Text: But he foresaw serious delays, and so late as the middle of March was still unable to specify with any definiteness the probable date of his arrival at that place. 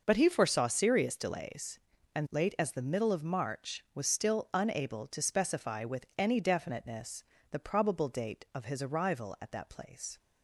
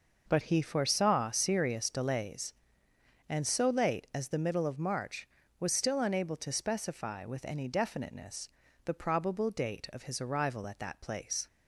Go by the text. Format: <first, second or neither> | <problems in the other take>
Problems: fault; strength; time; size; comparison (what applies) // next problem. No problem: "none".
second | skips "so"; at 2.2 s // pauses between "definiteness" and "the"; slight; at 7.2 s; 0.28 s long; slight in the second